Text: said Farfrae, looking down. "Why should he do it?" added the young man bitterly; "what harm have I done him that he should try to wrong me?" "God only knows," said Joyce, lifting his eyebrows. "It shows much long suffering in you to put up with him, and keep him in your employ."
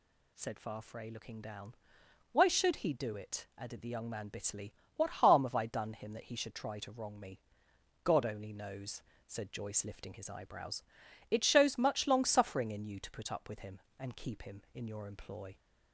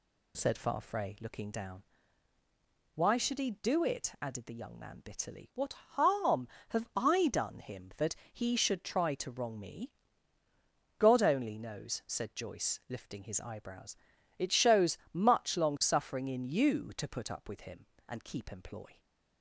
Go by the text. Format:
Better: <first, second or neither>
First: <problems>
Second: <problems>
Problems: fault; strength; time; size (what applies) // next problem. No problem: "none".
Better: first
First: none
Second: pauses between "that" and "he"; slight; at 8.1 s; 0.16 s long // pauses between "shows" and "much"; slight; at 14.9 s; 0.16 s long // skips "him in your"; at 18.4 s